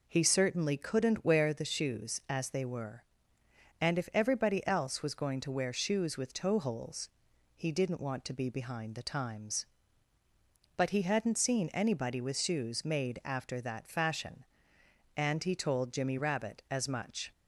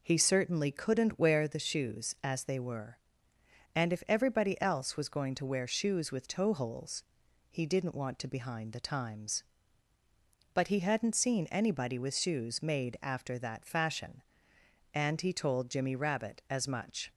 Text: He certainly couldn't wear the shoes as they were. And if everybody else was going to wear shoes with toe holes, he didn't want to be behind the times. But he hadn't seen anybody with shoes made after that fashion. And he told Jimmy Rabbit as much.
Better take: first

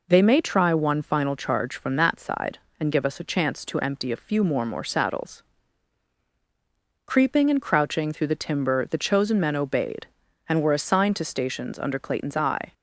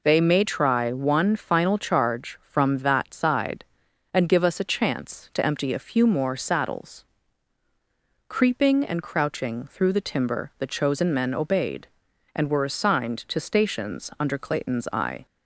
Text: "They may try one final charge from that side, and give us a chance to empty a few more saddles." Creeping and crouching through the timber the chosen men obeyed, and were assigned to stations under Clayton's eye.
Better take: second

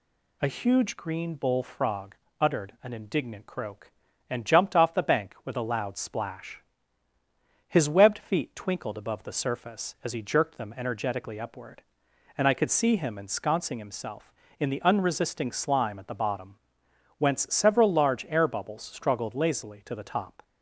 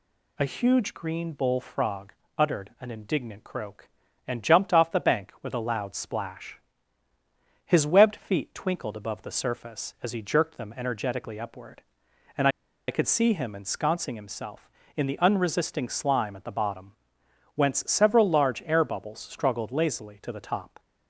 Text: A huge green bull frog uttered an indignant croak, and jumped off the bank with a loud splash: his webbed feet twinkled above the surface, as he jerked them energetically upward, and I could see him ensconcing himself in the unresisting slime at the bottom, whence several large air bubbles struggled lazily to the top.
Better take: first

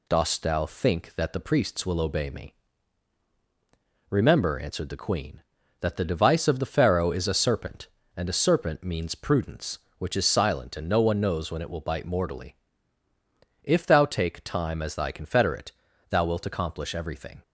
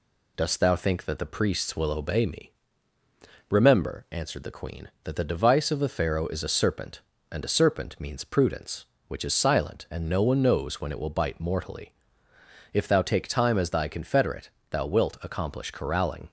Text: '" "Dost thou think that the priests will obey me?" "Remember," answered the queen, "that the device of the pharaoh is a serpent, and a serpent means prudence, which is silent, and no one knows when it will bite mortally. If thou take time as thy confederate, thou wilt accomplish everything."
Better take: first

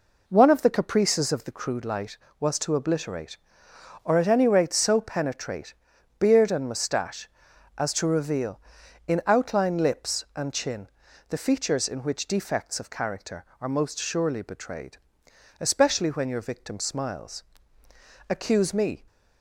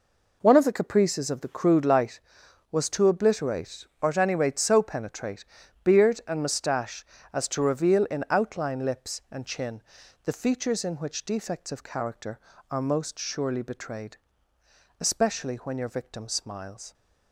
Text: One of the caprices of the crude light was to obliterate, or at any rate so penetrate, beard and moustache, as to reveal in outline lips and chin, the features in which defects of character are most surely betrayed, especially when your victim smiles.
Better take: second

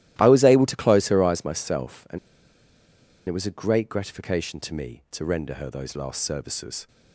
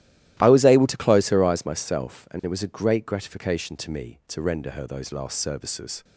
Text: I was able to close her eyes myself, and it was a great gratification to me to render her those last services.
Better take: second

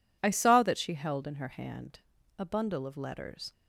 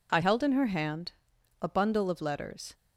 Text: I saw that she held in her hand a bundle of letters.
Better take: first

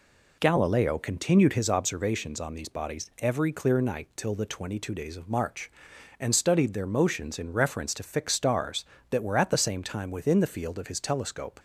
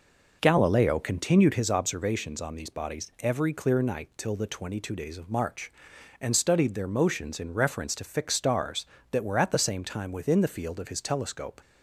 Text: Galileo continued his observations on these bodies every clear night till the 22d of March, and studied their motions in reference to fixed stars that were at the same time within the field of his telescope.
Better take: first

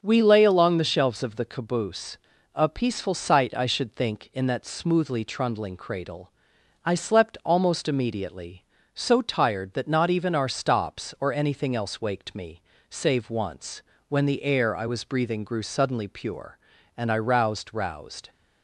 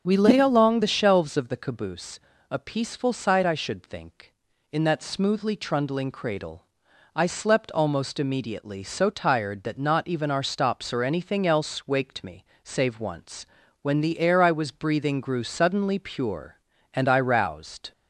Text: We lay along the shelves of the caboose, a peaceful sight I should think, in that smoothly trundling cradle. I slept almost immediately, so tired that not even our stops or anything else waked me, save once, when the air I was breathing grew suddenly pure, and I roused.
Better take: second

